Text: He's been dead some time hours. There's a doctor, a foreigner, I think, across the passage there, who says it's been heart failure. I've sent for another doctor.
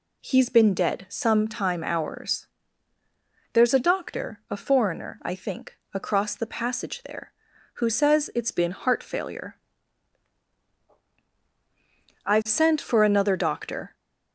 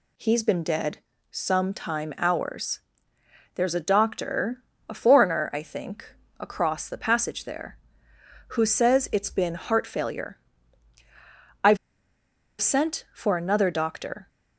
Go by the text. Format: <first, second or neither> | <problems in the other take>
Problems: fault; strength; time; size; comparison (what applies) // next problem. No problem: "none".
first | pauses between "dead" and "some"; slight; at 0.9 s; 0.32 s long // pauses between "I've" and "sent"; noticeable; at 11.7 s; 0.84 s long